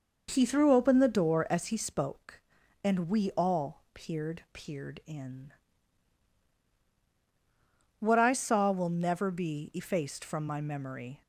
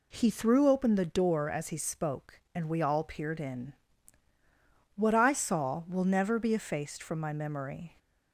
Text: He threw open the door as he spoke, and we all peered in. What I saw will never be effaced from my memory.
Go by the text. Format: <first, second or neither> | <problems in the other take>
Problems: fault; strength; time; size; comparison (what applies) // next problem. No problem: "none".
second | says "peered" twice; at 4.5 s